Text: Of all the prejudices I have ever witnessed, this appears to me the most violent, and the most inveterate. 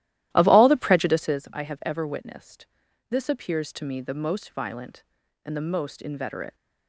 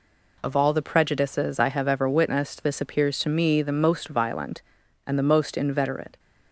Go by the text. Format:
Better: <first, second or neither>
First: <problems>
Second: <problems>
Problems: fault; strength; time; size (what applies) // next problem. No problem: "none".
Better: second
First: starts louder than the rest; strong; until 1.5 s; 14 dB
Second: none